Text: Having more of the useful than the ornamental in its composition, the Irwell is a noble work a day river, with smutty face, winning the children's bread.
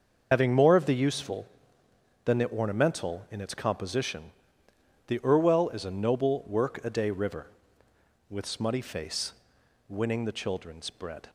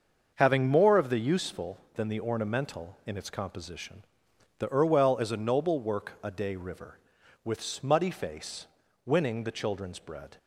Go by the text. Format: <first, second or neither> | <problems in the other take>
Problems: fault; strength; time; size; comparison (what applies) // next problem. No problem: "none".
second | loses the start of "Having"; at 0.3 s; 55 ms // starts louder than the rest; until 1.3 s; 6.5 dB; also in the second